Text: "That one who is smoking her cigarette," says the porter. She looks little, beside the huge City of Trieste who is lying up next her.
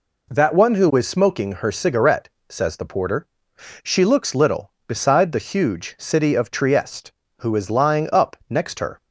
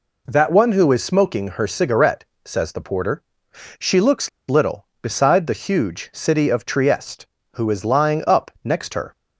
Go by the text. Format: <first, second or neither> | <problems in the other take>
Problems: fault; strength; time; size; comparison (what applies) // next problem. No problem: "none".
first | pauses between "looks" and "little"; slight; at 4.2 s; 0.20 s long